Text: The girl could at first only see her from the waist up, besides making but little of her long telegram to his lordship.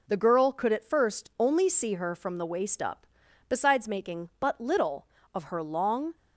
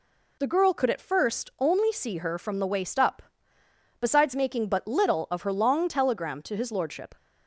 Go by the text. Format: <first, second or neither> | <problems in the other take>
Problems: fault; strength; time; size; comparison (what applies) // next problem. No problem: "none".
second | stops before "telegram to his lordship"; at 6.1 s